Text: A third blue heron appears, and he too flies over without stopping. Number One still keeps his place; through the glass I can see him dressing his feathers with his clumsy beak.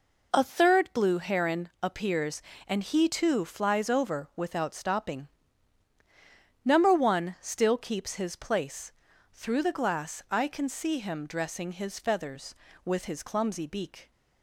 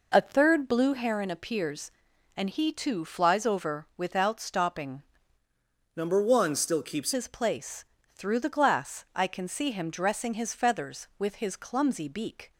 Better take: first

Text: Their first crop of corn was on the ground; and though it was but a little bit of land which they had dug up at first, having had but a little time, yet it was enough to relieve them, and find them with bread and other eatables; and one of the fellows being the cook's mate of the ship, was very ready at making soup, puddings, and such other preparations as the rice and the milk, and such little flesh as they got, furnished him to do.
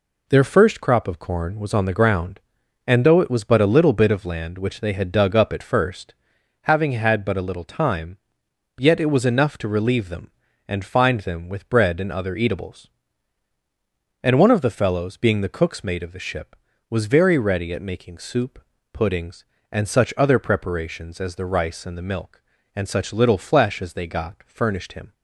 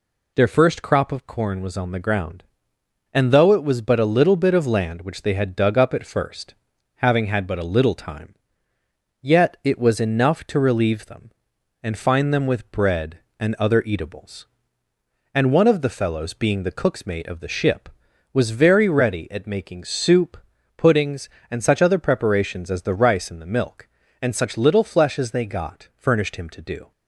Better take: second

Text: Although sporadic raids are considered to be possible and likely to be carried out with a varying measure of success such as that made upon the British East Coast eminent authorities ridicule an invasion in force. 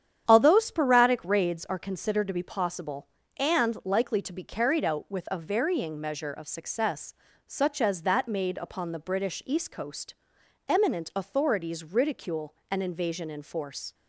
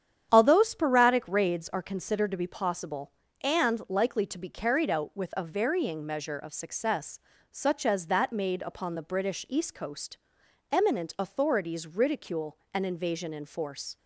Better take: neither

